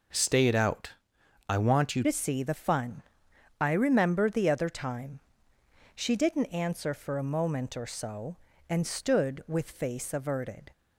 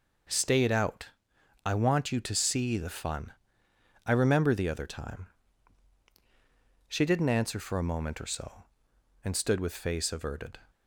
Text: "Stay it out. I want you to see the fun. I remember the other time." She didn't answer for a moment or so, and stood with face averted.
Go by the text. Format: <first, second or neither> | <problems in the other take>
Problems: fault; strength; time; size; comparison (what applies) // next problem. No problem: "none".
second | changes voice at "to"; from 2.0 s on; 8.7 s long